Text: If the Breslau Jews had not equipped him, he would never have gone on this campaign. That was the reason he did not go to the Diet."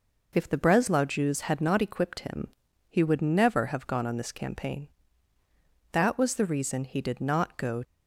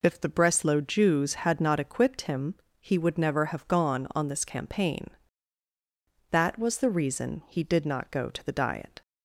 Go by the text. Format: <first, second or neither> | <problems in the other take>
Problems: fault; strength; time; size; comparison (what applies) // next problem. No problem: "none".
second | stops before "to the Diet"; at 7.8 s